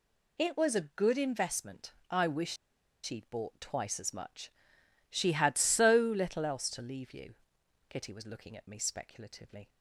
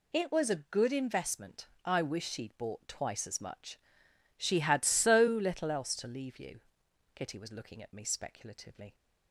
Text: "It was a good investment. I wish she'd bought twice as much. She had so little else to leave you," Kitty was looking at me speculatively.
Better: second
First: pauses between "wish" and "she'd"; noticeable; at 2.5 s; 0.48 s long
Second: none

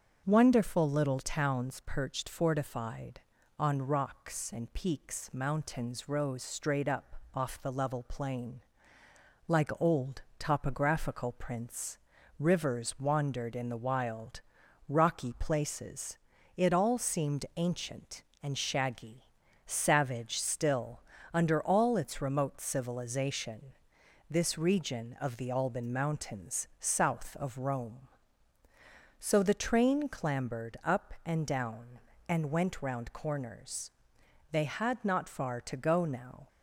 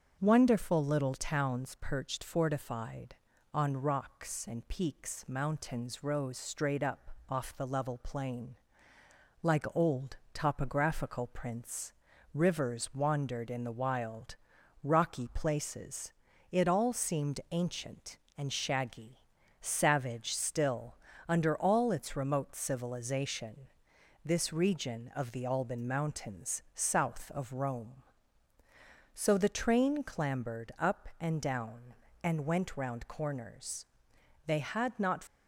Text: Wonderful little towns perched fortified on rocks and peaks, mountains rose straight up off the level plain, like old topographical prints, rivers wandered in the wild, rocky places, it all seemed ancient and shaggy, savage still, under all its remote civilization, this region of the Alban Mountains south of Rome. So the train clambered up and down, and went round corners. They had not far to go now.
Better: first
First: starts louder than the rest; until 1.2 s; 6.5 dB // pauses between "up" and "off"; slight; at 7.1 s; 0.16 s long // pauses between "old" and "topographical"; slight; at 10.2 s; 0.16 s long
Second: starts louder than the rest; until 1.2 s; 6.5 dB // pauses between "up" and "off"; slight; at 7.1 s; 0.16 s long // pauses between "old" and "topographical"; slight; at 10.1 s; 0.16 s long // stops before "far to go now"; at 35.2 s

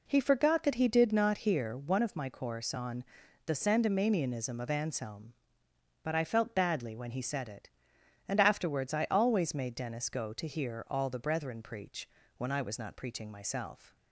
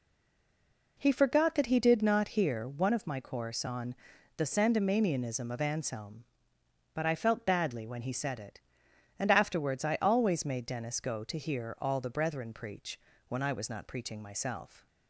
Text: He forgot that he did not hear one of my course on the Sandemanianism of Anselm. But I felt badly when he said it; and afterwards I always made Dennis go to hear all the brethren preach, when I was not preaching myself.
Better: first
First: pauses between "on" and "the"; at 3.0 s; 0.42 s long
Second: stays silent before the first word; until 0.9 s; 0.9 s long // pauses between "on" and "the"; at 3.9 s; 0.42 s long

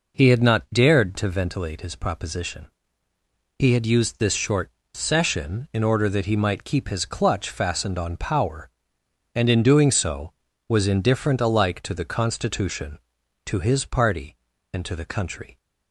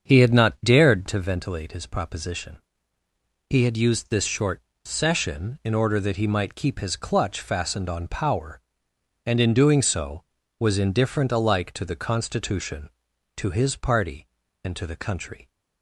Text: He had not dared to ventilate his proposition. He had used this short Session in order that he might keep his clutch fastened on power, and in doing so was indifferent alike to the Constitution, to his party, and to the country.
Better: first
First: pauses between "short" and "Session"; slight; at 4.7 s; 0.22 s long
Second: starts louder than the rest; until 1.2 s; 7 dB // pauses between "short" and "Session"; slight; at 4.6 s; 0.22 s long

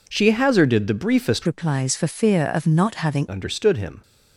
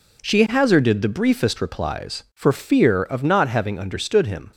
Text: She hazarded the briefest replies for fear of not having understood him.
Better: second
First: changes voice from "replies" to "having"; from 1.4 to 3.2 s; 1.8 s long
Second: none

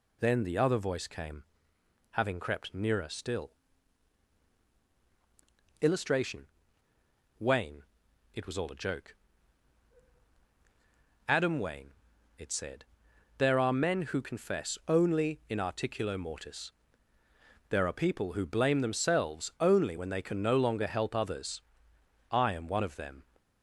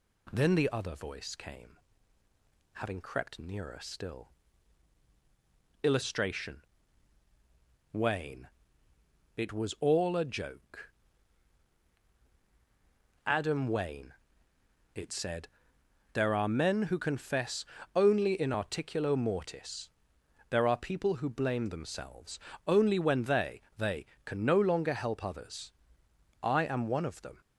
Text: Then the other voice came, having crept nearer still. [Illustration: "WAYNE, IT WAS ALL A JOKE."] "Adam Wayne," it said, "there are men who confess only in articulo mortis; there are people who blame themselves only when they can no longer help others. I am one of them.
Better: first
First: none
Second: pauses between "confess" and "only"; slight; at 17.6 s; 0.32 s long // pauses between "themselves" and "only"; slight; at 22.3 s; 0.28 s long // says "they" twice; at 23.7 s

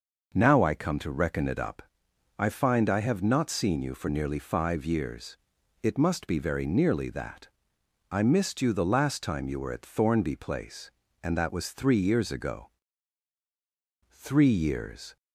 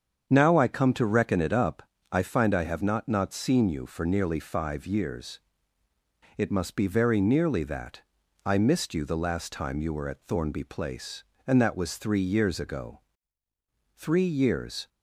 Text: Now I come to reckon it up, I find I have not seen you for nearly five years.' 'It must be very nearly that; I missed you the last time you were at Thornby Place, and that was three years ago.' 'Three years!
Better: first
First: none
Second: starts louder than the rest; strong; until 1.3 s; 7.5 dB // says "not" twice; at 3.0 s

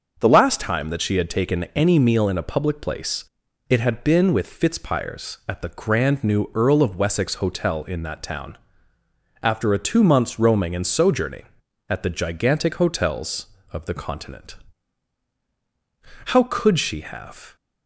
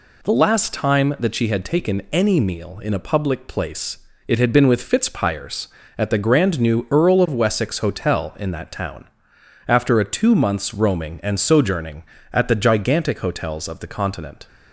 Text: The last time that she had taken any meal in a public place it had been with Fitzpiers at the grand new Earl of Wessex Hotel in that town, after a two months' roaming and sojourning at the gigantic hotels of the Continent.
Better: second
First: starts louder than the rest; until 1.2 s; 6 dB // pauses between "place" and "it"; at 3.2 s; 0.44 s long // goes on to say "How could she have"; noticeable; from 16.2 s on; 1.2 s long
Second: pauses between "place" and "it"; slight; at 3.9 s; 0.30 s long

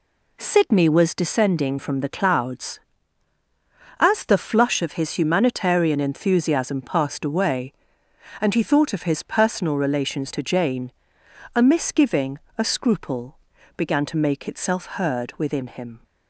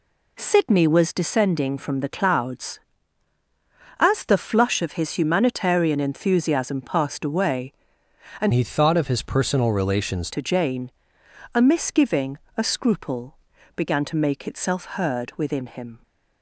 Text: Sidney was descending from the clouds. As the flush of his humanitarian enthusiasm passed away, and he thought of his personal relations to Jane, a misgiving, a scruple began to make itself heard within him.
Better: first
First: pauses between "scruple" and "began"; at 13.3 s; 0.40 s long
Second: changes voice from "he" to "relations"; from 8.5 to 10.3 s; 1.8 s long // pauses between "scruple" and "began"; at 13.3 s; 0.40 s long

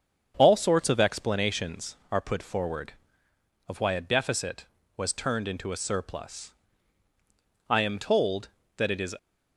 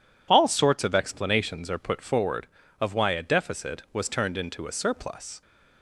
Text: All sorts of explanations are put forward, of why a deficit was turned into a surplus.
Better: second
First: starts louder than the rest; strong; until 1.3 s; 7.5 dB // goes on to say "I am told that it is"; from 7.6 s on; 1.4 s long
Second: none

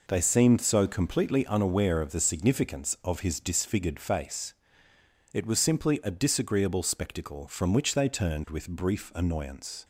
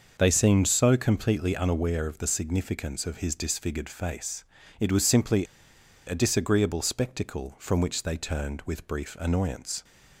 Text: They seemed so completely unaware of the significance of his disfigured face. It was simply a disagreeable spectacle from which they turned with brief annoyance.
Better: first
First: none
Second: starts louder than the rest; noticeable; until 1.2 s; 6 dB // pauses between "simply" and "a"; noticeable; at 5.4 s; 0.61 s long

